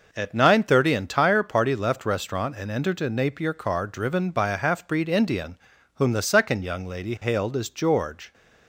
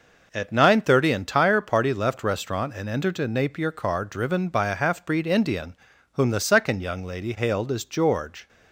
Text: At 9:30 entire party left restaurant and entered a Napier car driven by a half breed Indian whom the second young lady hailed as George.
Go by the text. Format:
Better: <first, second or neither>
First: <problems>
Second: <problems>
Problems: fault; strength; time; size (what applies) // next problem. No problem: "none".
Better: neither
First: pauses between "Indian" and "whom"; at 5.5 s; 0.38 s long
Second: pauses between "Indian" and "whom"; at 5.7 s; 0.38 s long